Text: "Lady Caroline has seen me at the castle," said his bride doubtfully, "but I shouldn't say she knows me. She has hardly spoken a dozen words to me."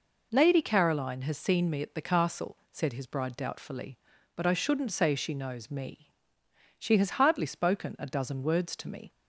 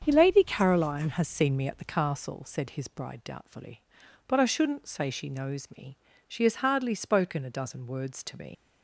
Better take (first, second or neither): first